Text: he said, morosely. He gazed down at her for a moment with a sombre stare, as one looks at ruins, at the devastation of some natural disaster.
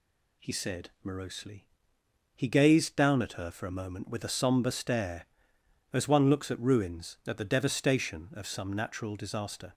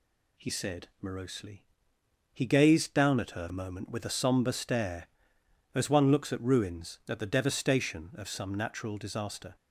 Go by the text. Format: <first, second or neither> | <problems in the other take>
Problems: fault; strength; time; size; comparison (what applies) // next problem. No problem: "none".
first | skips "for"; at 3.4 s